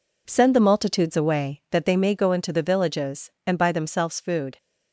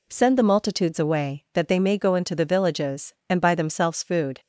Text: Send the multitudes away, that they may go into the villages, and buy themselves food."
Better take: second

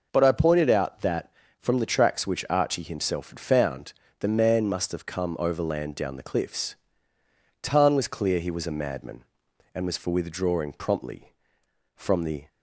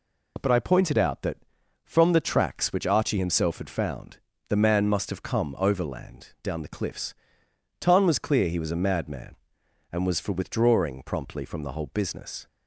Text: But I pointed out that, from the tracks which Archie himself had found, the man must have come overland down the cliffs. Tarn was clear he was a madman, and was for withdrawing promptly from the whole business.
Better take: second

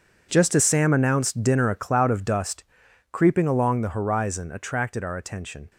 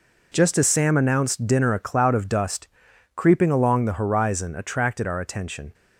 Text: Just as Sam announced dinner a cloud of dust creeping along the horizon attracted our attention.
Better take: second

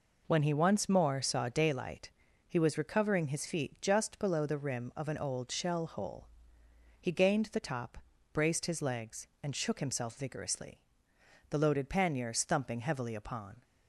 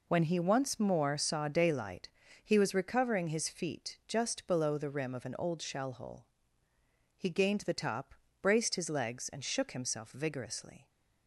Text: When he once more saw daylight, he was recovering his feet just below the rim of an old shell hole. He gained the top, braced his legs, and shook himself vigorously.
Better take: second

